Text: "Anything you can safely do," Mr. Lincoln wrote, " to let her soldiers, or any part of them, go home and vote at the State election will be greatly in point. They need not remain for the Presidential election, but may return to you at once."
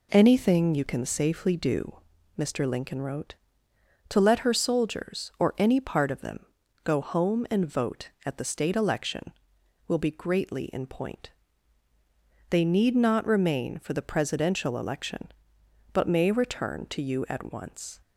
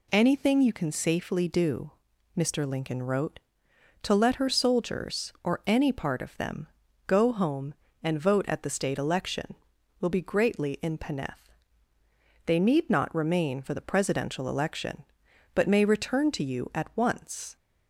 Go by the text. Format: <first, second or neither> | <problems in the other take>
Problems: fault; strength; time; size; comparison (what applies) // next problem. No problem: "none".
first | says "peneth" for "point"; at 10.9 s